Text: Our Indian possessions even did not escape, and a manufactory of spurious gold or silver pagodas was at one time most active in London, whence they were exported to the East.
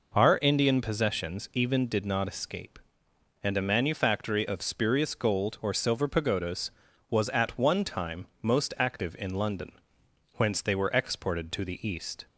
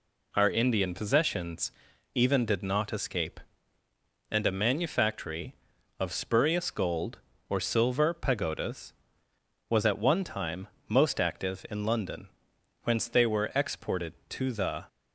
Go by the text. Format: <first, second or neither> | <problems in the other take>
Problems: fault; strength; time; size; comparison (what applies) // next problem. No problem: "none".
first | pauses between "possessions" and "even"; at 1.7 s; 0.42 s long // pauses between "time" and "most"; slight; at 10.6 s; 0.20 s long; slight in the first // stops before "East"; at 14.8 s